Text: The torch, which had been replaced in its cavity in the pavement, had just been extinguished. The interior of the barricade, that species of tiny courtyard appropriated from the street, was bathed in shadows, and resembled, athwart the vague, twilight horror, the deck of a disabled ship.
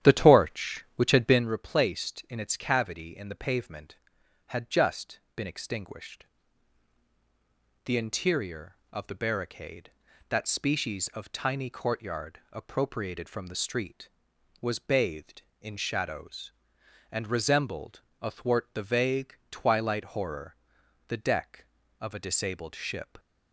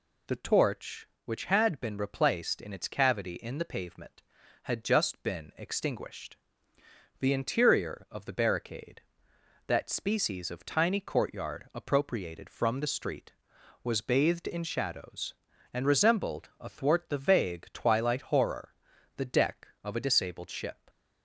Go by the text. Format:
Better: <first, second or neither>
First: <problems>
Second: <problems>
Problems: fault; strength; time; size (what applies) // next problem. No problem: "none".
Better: second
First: starts louder than the rest; strong; until 1.5 s; 10.5 dB // pauses between "just" and "been"; slight; at 5.1 s; 0.16 s long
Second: none